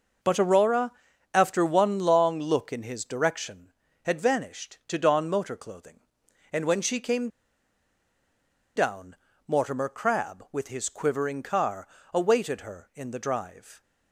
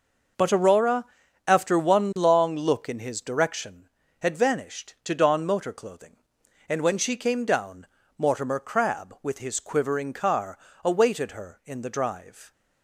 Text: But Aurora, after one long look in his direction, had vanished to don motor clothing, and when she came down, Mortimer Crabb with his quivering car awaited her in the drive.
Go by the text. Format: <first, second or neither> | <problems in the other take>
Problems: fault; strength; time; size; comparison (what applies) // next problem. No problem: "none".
second | pauses between "came" and "down"; strong; at 7.2 s; 1.4 s long // pauses between "car" and "awaited"; slight; at 11.8 s; 0.26 s long; slight in the second